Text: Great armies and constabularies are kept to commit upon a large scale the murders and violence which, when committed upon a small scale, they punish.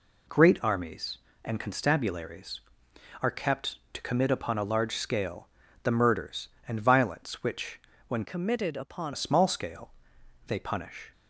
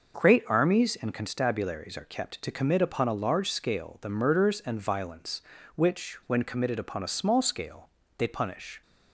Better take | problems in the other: second | pauses between "scale" and "the"; slight; at 5.4 s; 0.36 s long // changes voice from "committed" to "upon"; from 8.2 to 9.1 s; 0.9 s long

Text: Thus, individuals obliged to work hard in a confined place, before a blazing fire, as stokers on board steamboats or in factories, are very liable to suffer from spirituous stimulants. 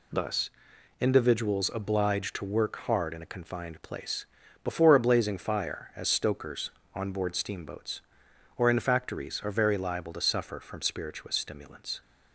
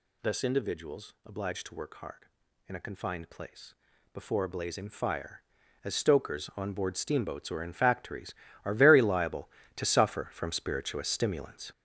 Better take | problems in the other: first | gets louder; strong; throughout; 7.5 dB

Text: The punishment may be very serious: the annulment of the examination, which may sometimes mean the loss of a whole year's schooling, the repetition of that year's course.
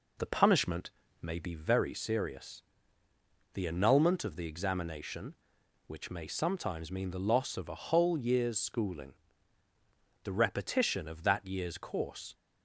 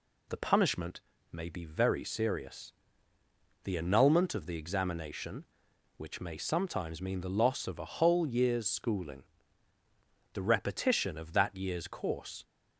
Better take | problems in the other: second | starts louder than the rest; until 1.8 s; 4 dB // pauses between "punishment" and "may"; slight; at 0.8 s; 0.32 s long; slight in the second

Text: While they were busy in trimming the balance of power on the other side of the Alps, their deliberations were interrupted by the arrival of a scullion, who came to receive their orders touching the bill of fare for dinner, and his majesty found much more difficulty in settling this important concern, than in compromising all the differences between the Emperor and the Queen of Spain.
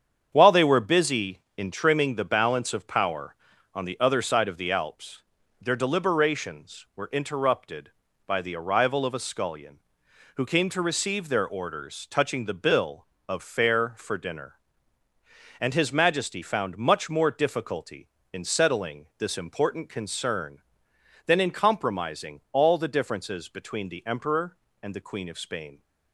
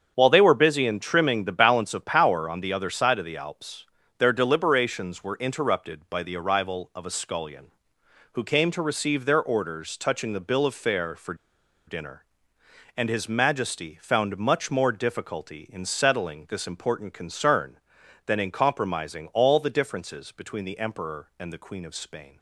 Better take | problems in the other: first | starts louder than the rest; strong; until 1.1 s; 7.5 dB; strong in the first // pauses between "for" and "dinner"; noticeable; at 11.3 s; 0.53 s long

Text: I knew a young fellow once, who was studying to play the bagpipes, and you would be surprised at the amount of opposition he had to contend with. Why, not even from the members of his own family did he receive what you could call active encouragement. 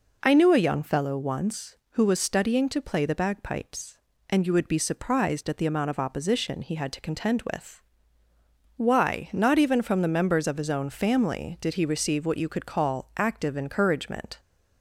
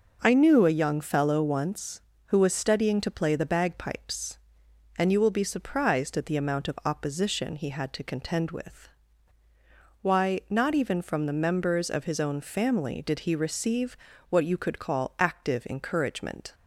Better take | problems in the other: first | says "will" for "would"; at 5.2 s // pauses between "receive" and "what"; slight; at 13.9 s; 0.34 s long

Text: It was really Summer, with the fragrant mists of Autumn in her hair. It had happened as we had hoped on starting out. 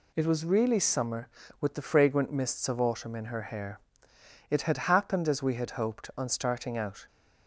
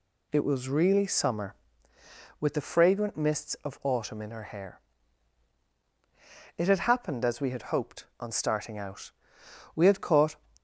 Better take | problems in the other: first | goes on to say "We had caught"; from 9.7 s on; 0.60 s long

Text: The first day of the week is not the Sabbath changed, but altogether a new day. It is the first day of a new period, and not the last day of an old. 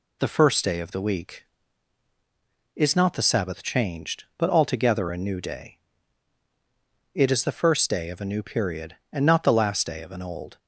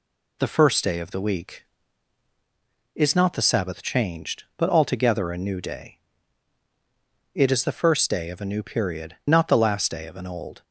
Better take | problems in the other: first | skips "and"; at 9.2 s

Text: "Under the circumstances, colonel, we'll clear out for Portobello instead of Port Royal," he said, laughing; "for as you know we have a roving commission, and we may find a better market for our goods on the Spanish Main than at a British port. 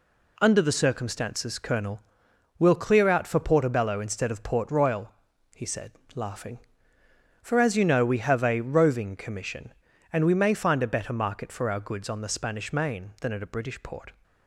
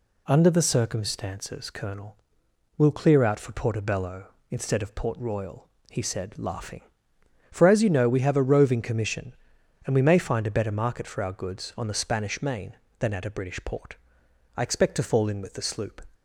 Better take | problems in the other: first | goes on to say "I expect to fall in with the sloop"; from 14.5 s on; 1.4 s long

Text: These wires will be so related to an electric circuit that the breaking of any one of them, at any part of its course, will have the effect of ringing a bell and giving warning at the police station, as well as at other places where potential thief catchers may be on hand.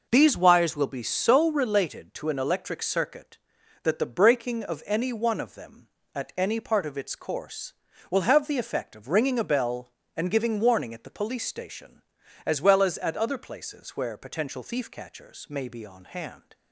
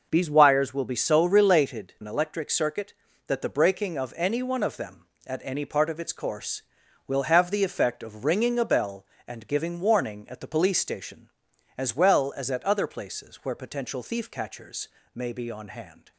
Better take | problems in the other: first | skips "to"; at 1.9 s // pauses between "catchers" and "may"; slight; at 14.8 s; 0.26 s long

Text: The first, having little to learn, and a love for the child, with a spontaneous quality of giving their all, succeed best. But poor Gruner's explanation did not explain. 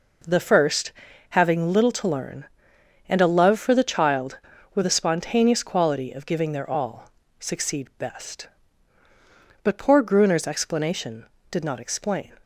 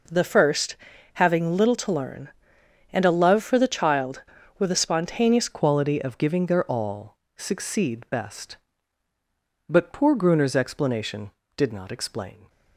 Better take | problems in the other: first | changes voice at "quality"; from 5.4 s on; 7.0 s long

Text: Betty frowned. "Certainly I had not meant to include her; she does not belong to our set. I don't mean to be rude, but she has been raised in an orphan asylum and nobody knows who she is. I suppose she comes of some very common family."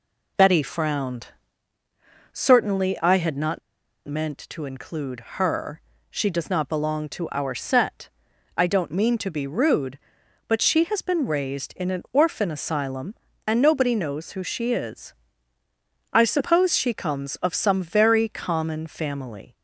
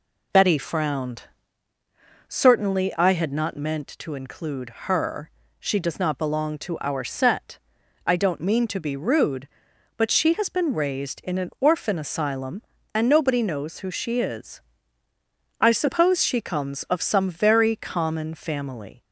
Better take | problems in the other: second | pauses between "not" and "meant"; noticeable; at 3.6 s; 0.47 s long

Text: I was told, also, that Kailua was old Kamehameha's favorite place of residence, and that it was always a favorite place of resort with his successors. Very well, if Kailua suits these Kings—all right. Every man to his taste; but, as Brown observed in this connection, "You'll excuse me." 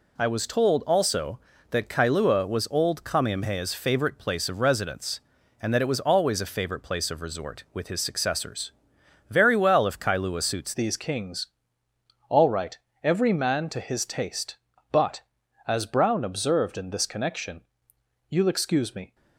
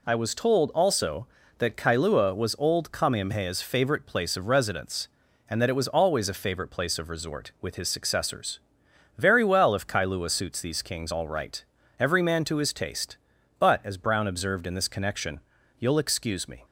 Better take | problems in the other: second | changes voice at "these"; from 10.7 s on; 8.4 s long

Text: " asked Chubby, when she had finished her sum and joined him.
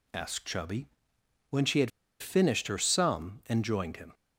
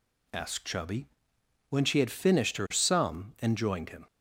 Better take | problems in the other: second | pauses between "had" and "finished"; slight; at 1.9 s; 0.30 s long

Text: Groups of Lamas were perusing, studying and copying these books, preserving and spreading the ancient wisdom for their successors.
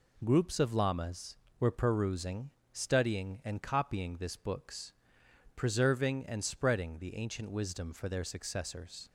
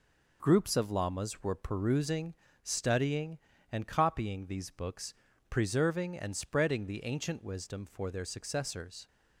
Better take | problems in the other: second | says "this" for "these"; at 4.1 s

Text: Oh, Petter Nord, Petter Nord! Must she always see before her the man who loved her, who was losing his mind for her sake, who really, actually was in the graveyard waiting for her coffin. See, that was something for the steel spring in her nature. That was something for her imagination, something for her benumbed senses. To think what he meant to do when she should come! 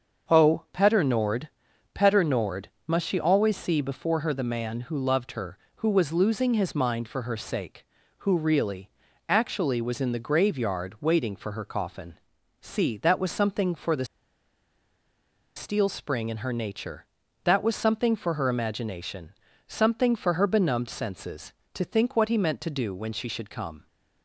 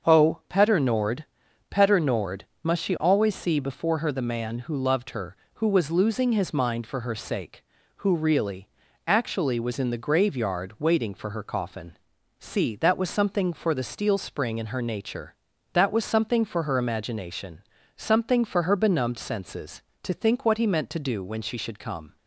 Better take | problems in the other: second | starts louder than the rest; until 1.4 s; 6.5 dB; also in the second // pauses between "the" and "steel"; strong; at 14.0 s; 1.5 s long

